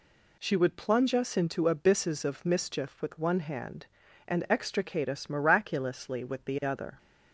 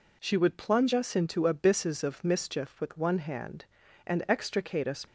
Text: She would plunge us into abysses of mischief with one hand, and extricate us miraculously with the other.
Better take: first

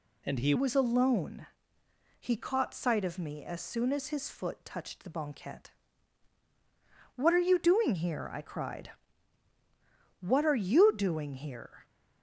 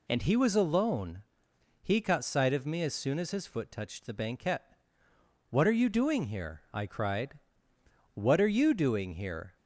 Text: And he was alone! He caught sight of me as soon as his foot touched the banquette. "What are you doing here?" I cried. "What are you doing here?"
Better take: second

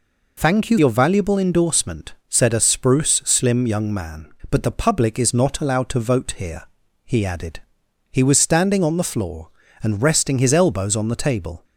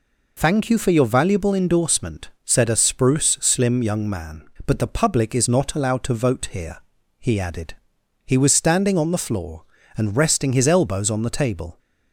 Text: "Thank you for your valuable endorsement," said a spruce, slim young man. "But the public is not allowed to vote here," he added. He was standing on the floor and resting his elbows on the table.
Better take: second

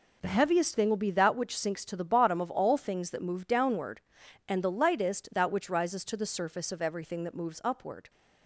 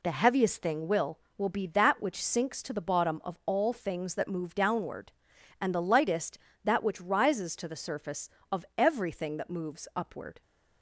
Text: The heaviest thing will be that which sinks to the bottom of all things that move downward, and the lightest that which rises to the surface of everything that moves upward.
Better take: first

